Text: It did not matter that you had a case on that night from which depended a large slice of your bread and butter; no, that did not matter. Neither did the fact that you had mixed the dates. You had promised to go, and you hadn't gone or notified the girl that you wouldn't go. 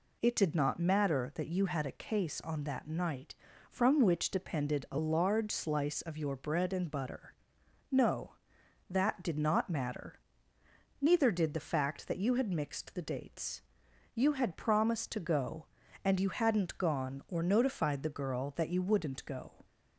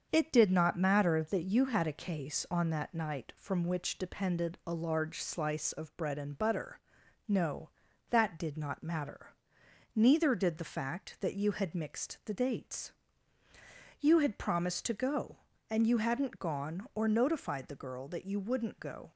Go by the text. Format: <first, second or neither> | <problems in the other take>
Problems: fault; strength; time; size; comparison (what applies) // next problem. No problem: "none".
first | starts louder than the rest; until 1.1 s; 7 dB // skips "your"; at 5.9 s